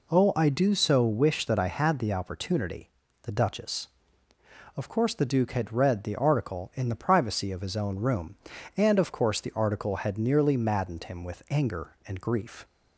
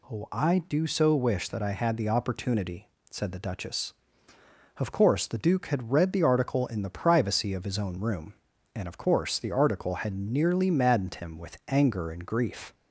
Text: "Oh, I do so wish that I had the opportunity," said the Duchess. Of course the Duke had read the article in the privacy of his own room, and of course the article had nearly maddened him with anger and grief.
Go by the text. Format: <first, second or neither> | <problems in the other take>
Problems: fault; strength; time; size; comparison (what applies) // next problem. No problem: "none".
second | skips "said"; at 3.0 s